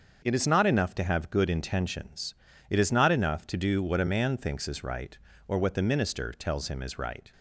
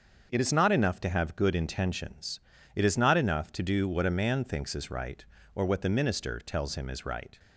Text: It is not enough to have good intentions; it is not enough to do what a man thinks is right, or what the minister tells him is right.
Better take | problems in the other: neither | starts louder than the rest; the same in both

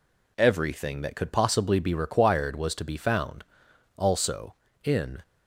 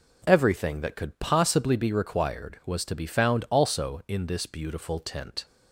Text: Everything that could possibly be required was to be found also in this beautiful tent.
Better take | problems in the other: second | pauses between "found" and "also"; noticeable; at 3.4 s; 0.52 s long // stops before "this beautiful tent"; at 5.2 s

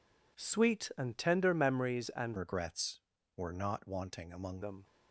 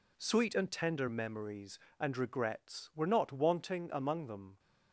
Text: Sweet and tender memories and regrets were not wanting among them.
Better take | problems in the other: second | changes voice from "regrets" to "among"; from 2.3 to 4.6 s; 2.3 s long

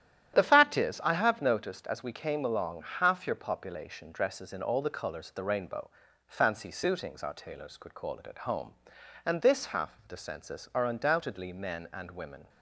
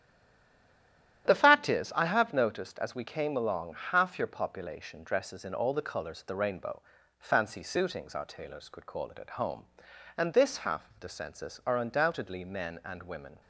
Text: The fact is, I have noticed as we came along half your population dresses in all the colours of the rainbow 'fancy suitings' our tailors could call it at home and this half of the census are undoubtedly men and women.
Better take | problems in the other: first | stays silent before the first word; noticeable; until 1.2 s; 1.2 s long // starts louder than the rest; strong; until 2.3 s; 11 dB; strong in the first // pauses between "along" and "half"; slight; at 3.7 s; 0.16 s long; slight in the first // pauses between "rainbow" and "fancy"; slight; at 6.8 s; 0.36 s long; slight in the first

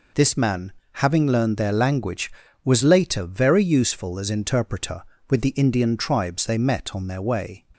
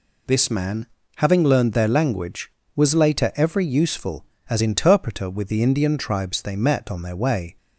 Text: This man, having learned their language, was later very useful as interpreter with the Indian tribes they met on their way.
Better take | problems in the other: first | says "every" for "very"; at 3.3 s

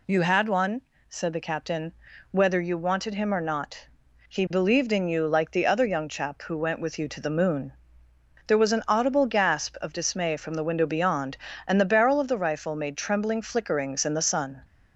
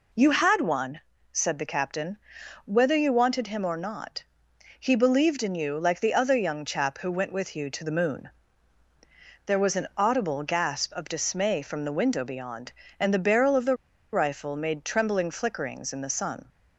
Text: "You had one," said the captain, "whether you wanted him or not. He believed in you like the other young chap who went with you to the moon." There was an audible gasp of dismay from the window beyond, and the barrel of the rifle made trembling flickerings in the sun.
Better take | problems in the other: first | pauses between "the" and "rifle"; at 13.7 s; 0.36 s long

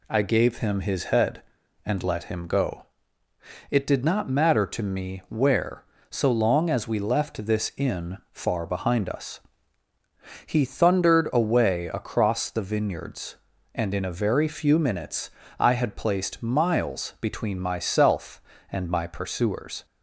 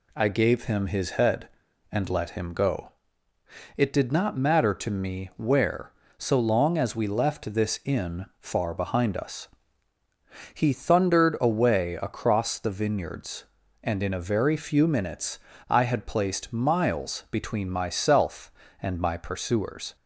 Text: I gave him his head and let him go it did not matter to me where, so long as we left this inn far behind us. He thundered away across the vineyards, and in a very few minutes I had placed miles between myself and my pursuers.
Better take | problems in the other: neither | pauses between "go" and "it"; noticeable; the same in both // pauses between "minutes" and "I"; slight; the same in both

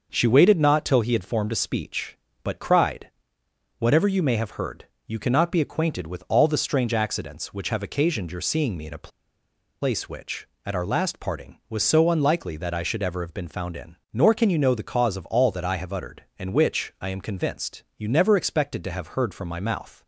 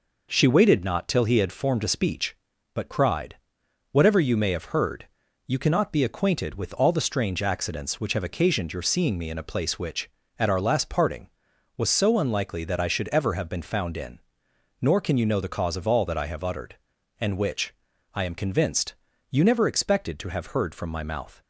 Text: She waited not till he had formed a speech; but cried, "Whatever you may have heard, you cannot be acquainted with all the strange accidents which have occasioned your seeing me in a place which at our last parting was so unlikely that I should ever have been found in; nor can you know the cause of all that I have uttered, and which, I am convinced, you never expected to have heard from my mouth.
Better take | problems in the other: second | pauses between "a" and "place"; noticeable; at 9.0 s; 0.73 s long

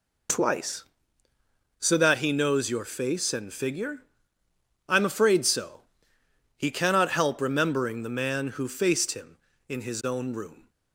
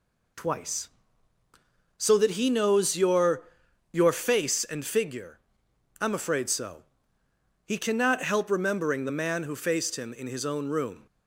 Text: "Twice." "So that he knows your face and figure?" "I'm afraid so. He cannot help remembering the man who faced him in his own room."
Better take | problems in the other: first | says "your" twice; at 3.9 s

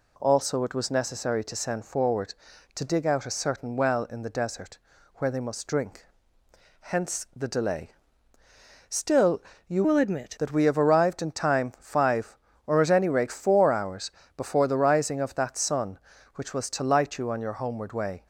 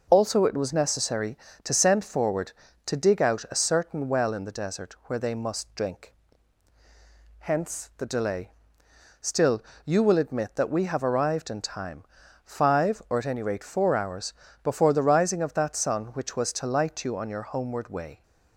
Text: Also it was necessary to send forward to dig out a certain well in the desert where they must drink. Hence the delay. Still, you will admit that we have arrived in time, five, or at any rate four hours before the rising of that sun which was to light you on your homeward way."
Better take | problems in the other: second | pauses between "desert" and "where"; at 4.7 s; 0.38 s long // changes voice from "will" to "admit"; from 9.8 to 10.3 s; 0.5 s long // pauses between "hours" and "before"; slight; at 14.0 s; 0.26 s long; slight in the second

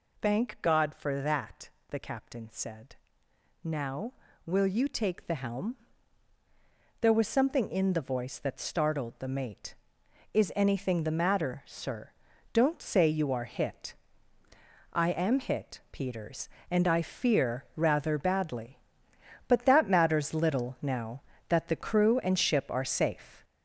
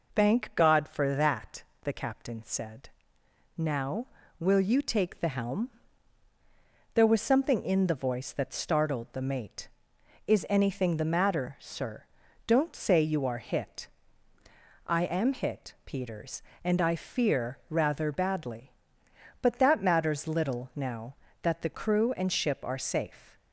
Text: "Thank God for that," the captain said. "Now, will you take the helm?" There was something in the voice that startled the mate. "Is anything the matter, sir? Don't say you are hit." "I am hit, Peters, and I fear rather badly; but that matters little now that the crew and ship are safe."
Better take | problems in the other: second | gets louder; noticeable; throughout; 5.5 dB

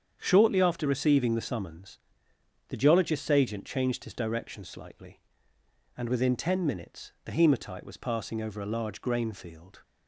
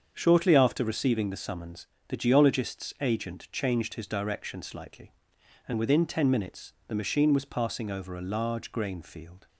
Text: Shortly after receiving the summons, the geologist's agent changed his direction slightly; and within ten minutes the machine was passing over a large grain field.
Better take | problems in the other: second | starts louder than the rest; strong; until 1.2 s; 8 dB; also in the second // says "hematite" for "machine"; at 7.3 s

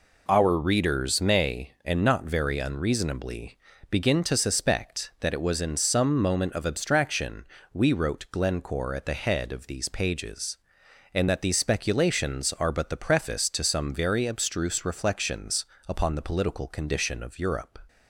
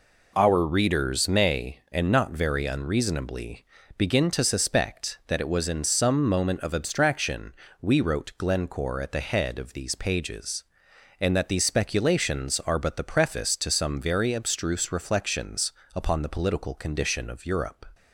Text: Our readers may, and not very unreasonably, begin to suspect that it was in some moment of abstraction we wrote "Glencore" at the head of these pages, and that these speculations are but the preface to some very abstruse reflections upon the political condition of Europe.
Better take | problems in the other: neither | pauses between "abstraction" and "we"; slight; the same in both // pauses between "reflections" and "upon"; slight; the same in both

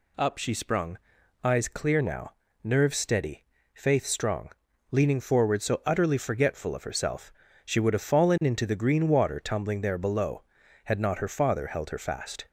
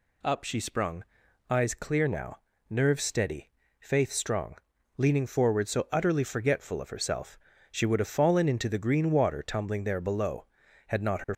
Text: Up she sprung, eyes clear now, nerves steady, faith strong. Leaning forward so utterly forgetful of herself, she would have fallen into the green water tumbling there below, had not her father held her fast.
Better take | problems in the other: first | stops before "father held her fast"; at 11.3 s

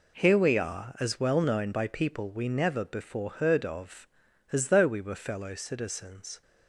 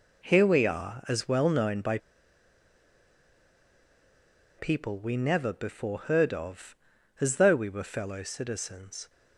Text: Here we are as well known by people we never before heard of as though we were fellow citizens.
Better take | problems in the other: first | pauses between "by" and "people"; strong; at 1.9 s; 2.6 s long

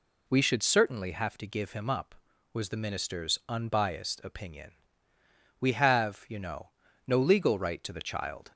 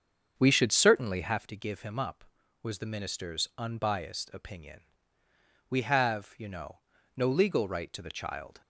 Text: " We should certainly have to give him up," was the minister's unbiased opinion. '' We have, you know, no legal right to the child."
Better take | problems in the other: first | starts louder than the rest; strong; until 1.6 s; 7 dB

